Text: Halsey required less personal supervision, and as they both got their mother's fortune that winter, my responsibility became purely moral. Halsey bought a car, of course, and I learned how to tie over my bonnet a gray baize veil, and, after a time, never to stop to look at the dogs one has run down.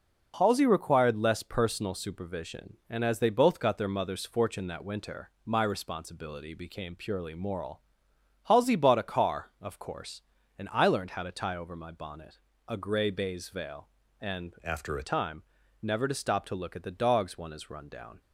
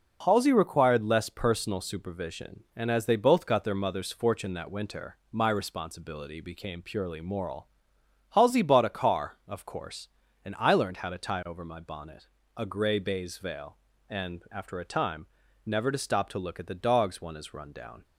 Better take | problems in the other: second | pauses between "bonnet" and "a"; slight; at 12.3 s; 0.28 s long; slight in the second // changes voice from "after" to "a"; from 14.6 to 15.0 s; 0.4 s long

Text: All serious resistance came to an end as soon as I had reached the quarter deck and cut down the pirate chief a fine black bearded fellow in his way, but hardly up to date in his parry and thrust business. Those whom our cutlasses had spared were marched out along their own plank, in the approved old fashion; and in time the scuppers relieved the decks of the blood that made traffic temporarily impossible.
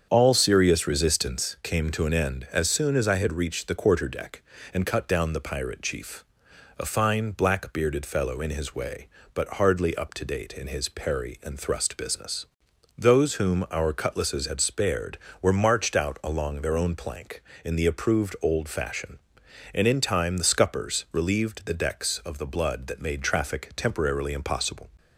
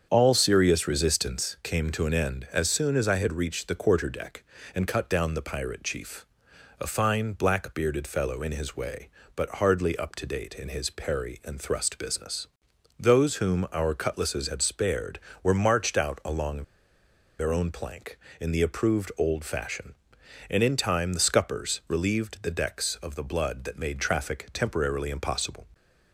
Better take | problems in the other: first | starts louder than the rest; strong; until 1.1 s; 7.5 dB; strong in the first // pauses between "chief" and "a"; noticeable; at 6.2 s; 0.56 s long; noticeable in the first // pauses between "along" and "their"; noticeable; at 16.6 s; 0.76 s long

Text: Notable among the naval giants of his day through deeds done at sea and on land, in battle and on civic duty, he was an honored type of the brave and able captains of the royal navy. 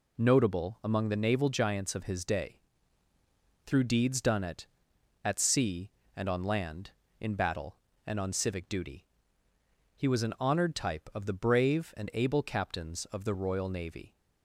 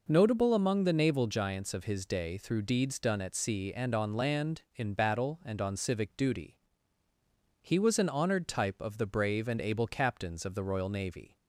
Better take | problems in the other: second | pauses between "day" and "through"; at 2.5 s; 1.0 s long // says "at" twice; at 5.2 s

